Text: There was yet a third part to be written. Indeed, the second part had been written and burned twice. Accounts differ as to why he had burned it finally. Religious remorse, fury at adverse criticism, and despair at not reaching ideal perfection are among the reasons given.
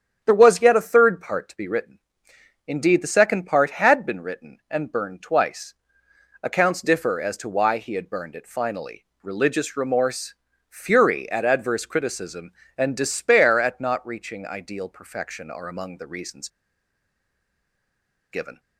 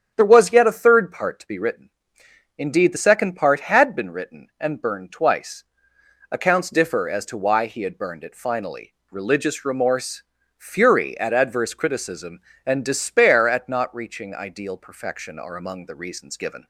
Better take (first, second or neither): second